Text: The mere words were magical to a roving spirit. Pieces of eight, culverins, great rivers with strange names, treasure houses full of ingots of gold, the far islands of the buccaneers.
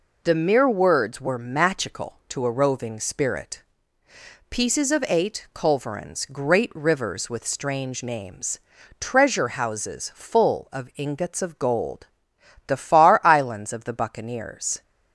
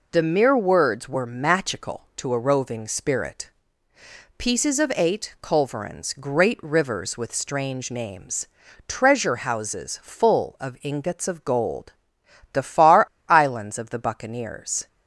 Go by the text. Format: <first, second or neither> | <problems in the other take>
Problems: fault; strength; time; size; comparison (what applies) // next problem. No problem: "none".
first | pauses between "far" and "islands"; slight; at 13.0 s; 0.23 s long